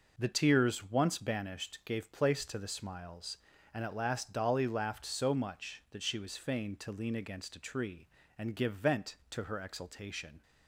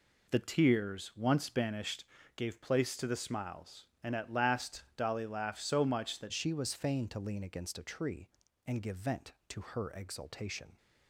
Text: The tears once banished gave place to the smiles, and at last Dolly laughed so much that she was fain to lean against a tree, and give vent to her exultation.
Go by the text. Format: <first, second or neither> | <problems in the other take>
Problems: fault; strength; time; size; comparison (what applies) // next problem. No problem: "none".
first | pauses between "banished" and "gave"; slight; at 2.0 s; 0.32 s long // pauses between "last" and "Dolly"; slight; at 4.8 s; 0.16 s long // changes voice at "she"; from 6.3 s on; 4.4 s long